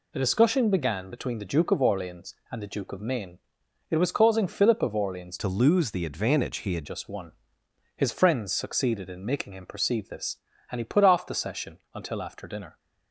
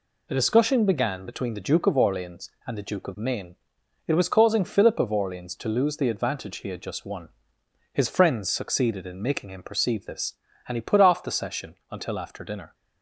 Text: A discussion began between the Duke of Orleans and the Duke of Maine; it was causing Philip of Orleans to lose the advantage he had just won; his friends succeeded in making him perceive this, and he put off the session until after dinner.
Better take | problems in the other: second | changes voice from "to" to "had"; from 5.3 to 6.8 s; 1.5 s long // pauses between "session" and "until"; slight; at 11.7 s; 0.16 s long; slight in the second

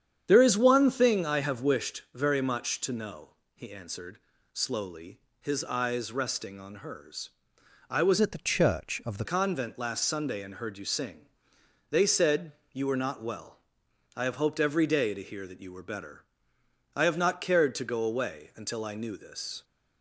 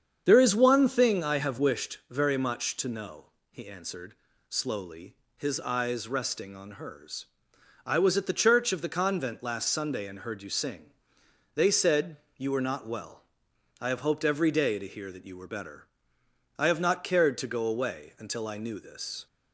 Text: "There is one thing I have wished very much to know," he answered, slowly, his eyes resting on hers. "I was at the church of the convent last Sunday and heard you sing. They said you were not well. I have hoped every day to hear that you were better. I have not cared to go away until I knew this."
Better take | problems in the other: second | starts louder than the rest; strong; until 1.2 s; 8.5 dB; strong in the second // changes voice from "at" to "the"; from 8.2 to 9.2 s; 1.0 s long // pauses between "said" and "you"; slight; at 12.5 s; 0.20 s long; slight in the second

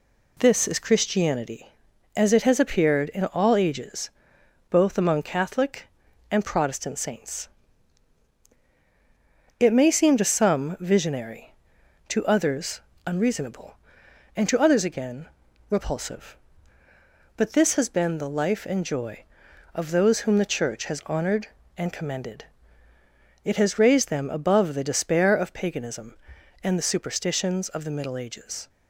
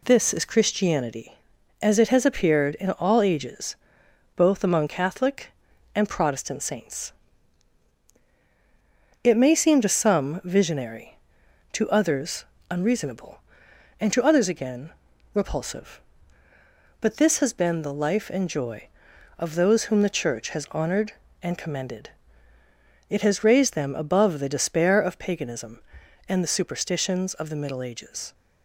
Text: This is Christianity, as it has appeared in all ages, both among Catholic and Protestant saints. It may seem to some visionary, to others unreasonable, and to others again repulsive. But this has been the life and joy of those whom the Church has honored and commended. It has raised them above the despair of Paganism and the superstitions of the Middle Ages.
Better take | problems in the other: neither | pauses between "others" and "unreasonable"; slight; the same in both // pauses between "again" and "repulsive"; the same in both

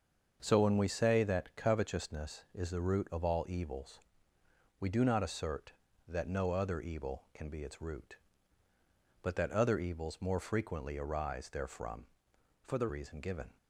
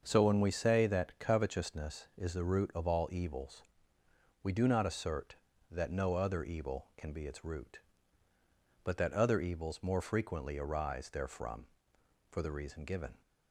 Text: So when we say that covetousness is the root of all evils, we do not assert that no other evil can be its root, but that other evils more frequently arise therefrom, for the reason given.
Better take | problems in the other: second | starts louder than the rest; until 1.4 s; 6.5 dB; also in the second // changes voice from "for" to "the"; from 12.6 to 12.8 s; 0.2 s long

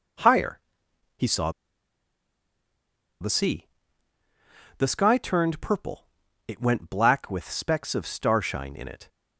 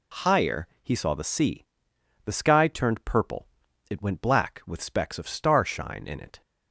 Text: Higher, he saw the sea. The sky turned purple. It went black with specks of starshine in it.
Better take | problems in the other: second | pauses between "saw" and "the"; strong; at 1.5 s; 1.6 s long

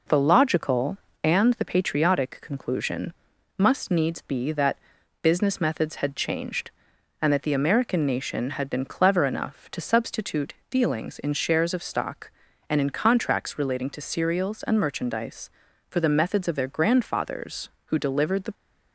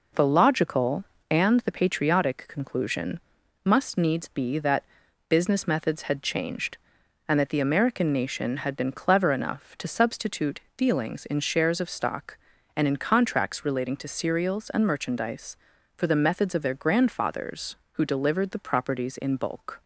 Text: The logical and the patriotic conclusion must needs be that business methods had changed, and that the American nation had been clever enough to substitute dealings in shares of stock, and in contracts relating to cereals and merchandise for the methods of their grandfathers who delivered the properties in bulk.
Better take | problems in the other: second | pauses between "conclusion" and "must"; noticeable; at 3.1 s; 0.46 s long; noticeable in the second // pauses between "that" and "business"; at 4.7 s; 0.44 s long; also in the second // pauses between "substitute" and "dealings"; slight; at 10.5 s; 0.16 s long; slight in the second // stops before "properties in bulk"; at 18.5 s

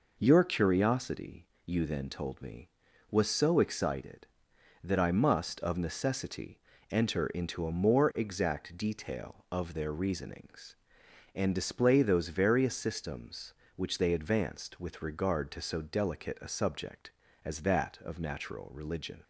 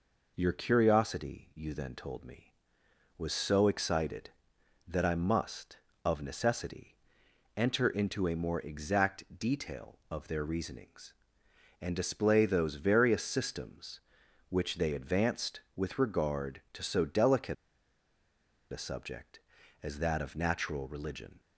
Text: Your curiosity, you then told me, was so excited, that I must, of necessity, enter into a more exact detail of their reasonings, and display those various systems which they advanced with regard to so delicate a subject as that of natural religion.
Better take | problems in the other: first | pauses between "delicate" and "a"; at 17.5 s; 1.1 s long

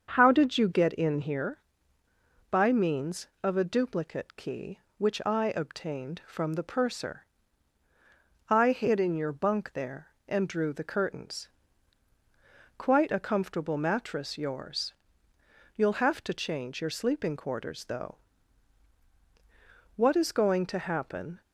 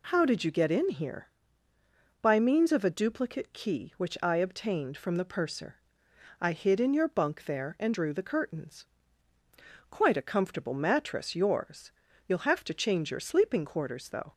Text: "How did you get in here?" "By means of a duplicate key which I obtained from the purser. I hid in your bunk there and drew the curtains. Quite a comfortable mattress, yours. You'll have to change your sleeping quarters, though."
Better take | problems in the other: second | starts louder than the rest; until 1.1 s; 7 dB // goes on to say "What is going to happen"; from 19.9 s on; 1.4 s long

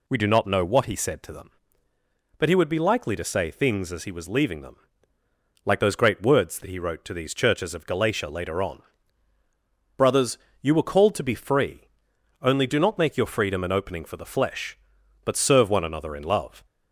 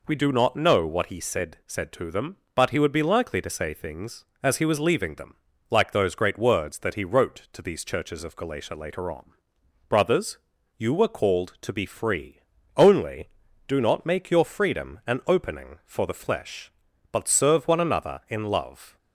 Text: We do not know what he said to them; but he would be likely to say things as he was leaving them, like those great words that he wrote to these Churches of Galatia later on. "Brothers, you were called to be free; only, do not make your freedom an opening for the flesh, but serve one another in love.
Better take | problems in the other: first | says "said" twice; at 1.6 s

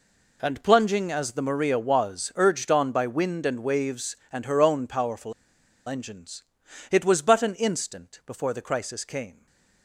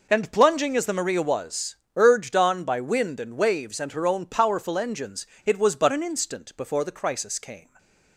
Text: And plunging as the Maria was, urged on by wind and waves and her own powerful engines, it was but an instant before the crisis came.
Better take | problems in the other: second | pauses between "powerful" and "engines"; noticeable; at 5.3 s; 0.54 s long // stays silent after the last word; slight; from 9.3 s on; 0.5 s long

